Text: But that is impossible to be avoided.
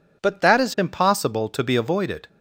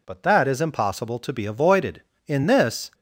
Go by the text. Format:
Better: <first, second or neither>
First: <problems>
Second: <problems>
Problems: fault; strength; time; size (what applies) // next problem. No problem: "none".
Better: first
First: none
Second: goes on to say "In this"; noticeable; from 2.2 s on; 0.62 s long